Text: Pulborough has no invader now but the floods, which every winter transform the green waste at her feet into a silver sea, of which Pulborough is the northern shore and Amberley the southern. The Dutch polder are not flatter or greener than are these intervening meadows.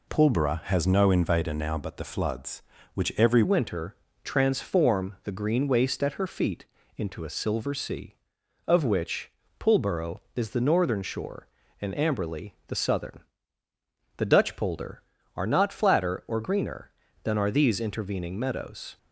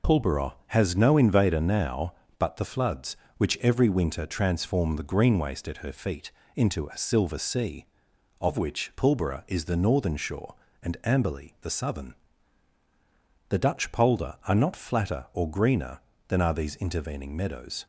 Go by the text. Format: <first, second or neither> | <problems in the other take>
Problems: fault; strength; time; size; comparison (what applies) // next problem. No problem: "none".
second | changes voice at "winter"; from 3.4 s on; 15.5 s long // pauses between "winter" and "transform"; slight; at 3.9 s; 0.28 s long // pauses between "feet" and "into"; slight; at 6.6 s; 0.32 s long; slight in the second // pauses between "which" and "Pulborough"; slight; at 9.3 s; 0.28 s long